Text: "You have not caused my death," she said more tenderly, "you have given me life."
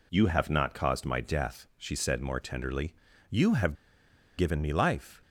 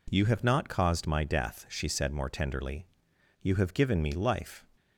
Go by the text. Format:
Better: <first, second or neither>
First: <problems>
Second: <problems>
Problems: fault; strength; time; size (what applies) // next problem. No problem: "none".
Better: second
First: pauses between "have" and "given"; noticeable; at 3.7 s; 0.62 s long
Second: none